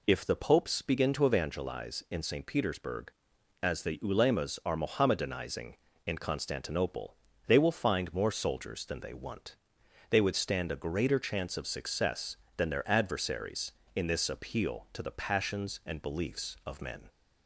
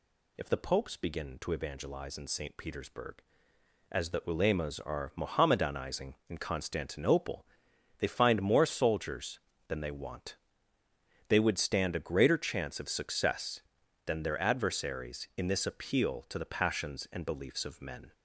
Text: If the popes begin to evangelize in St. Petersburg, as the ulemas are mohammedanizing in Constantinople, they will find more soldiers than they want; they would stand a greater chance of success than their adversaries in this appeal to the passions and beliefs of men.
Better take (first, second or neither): first